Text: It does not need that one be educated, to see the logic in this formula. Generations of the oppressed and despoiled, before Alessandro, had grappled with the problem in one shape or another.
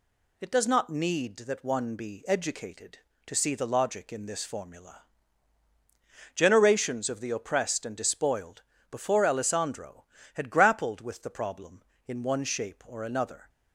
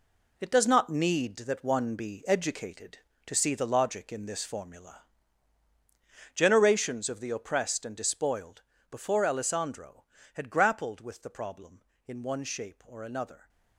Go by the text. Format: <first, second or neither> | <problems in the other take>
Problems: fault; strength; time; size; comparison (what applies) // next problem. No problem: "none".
first | gets quieter; strong; throughout; 8.5 dB